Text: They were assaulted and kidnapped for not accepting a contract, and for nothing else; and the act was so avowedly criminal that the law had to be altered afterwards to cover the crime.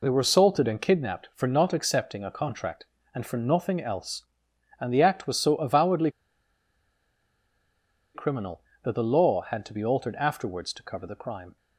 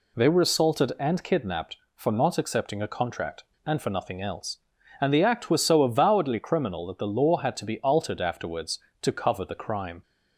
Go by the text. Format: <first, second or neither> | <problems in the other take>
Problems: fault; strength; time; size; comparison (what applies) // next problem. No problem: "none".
second | pauses between "avowedly" and "criminal"; strong; at 6.0 s; 2.0 s long